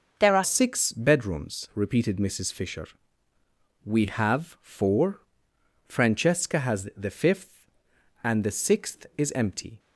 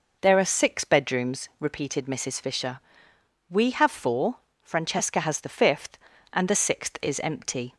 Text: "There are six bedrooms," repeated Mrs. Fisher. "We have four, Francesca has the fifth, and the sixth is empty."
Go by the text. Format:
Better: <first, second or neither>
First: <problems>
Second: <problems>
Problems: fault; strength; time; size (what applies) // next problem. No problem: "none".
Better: second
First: changes voice at "six"; from 0.4 s on; 9.3 s long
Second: none